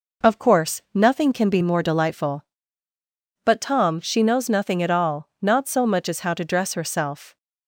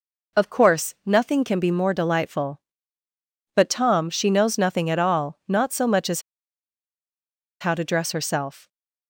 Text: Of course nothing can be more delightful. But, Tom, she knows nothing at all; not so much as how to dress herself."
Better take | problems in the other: first | pauses between "as" and "how"; strong; at 6.2 s; 1.3 s long

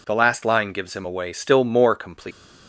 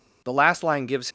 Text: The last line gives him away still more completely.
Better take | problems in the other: first | stops before "him away still more completely"; at 1.0 s

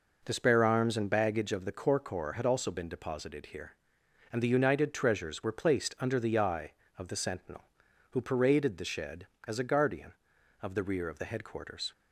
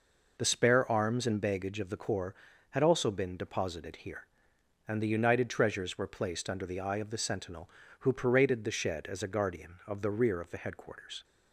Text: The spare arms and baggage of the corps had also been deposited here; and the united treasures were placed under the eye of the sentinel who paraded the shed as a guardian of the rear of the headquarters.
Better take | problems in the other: second | says "corps" twice; at 1.9 s

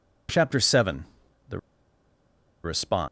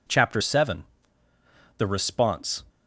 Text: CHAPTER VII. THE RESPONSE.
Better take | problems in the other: second | pauses between "THE" and "RESPONSE"; at 1.5 s; 1.0 s long

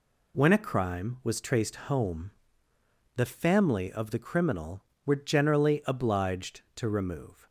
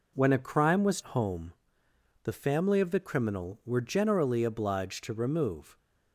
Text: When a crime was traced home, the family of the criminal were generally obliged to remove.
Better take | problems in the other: first | skips "traced"; at 1.0 s

